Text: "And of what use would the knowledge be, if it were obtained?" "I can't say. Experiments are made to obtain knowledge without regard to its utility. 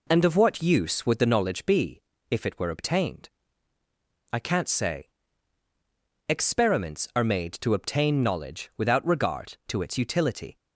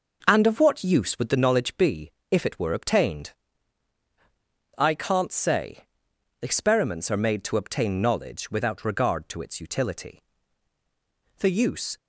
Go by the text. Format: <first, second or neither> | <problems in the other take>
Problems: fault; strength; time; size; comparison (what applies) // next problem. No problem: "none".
first | goes on to say "The use"; from 11.3 s on; 0.58 s long